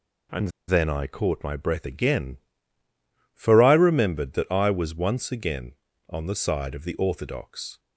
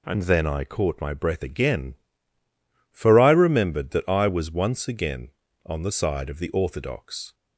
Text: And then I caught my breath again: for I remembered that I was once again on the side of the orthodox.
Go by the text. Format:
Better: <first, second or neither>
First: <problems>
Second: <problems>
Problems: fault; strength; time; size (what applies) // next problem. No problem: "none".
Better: second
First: pauses between "And" and "then"; slight; at 0.4 s; 0.19 s long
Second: none